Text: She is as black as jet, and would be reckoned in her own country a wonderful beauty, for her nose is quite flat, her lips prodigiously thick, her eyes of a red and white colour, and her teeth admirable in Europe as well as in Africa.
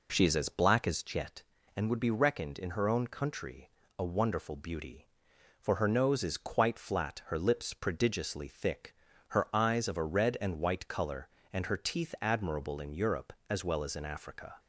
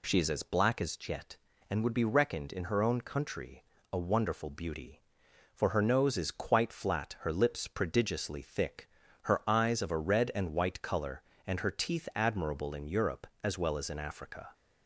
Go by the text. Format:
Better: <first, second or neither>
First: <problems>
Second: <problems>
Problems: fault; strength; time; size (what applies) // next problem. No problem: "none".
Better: second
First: starts louder than the rest; until 1.4 s; 4 dB // pauses between "country" and "a"; slight; at 3.6 s; 0.28 s long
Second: pauses between "country" and "a"; slight; at 3.6 s; 0.28 s long